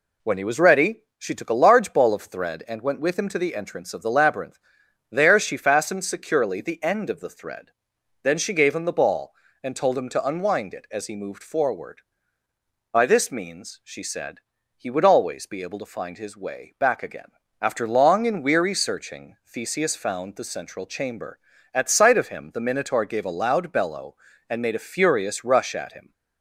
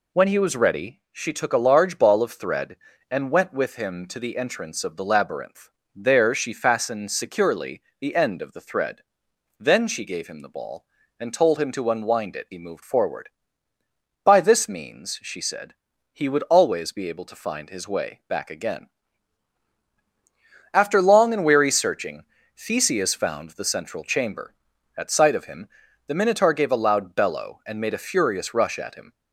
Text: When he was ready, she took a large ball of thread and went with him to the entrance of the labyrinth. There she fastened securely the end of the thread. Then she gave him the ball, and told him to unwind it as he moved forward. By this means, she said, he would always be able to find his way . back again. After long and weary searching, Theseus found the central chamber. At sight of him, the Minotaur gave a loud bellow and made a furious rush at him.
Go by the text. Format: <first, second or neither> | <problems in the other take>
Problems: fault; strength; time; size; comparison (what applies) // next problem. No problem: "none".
first | pauses between "securely" and "the"; slight; at 7.8 s; 0.18 s long // skips "as"; at 12.4 s